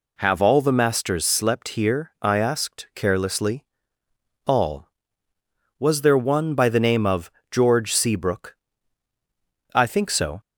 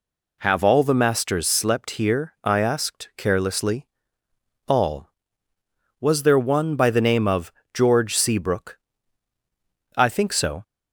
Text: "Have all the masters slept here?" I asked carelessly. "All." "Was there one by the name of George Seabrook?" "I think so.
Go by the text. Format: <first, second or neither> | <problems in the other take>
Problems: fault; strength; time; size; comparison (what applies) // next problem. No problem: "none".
neither | pauses between "of" and "George"; slight; the same in both